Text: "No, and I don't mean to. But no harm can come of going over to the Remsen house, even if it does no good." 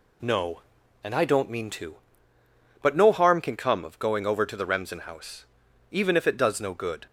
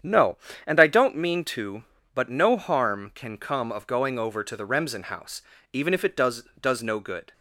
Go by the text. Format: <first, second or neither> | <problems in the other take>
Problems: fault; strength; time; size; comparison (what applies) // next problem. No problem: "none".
first | starts louder than the rest; strong; until 1.2 s; 8.5 dB // says "does" twice; at 6.5 s